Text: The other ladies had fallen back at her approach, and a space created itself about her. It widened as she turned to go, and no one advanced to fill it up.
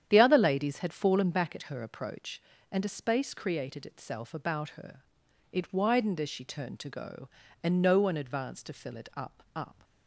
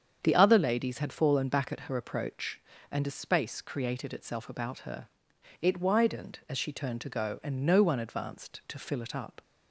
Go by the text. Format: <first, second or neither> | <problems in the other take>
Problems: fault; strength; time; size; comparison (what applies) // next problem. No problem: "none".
second | starts louder than the rest; strong; until 1.1 s; 9 dB; strong in the second // says "up" twice; at 9.5 s